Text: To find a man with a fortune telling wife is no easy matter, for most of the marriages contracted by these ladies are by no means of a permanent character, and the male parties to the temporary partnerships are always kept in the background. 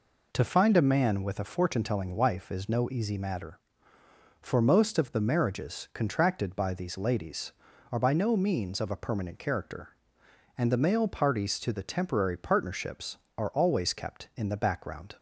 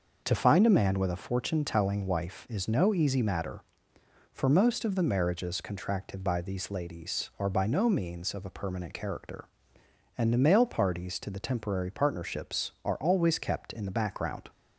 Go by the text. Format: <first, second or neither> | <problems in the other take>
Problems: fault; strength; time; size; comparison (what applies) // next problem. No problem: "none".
neither | none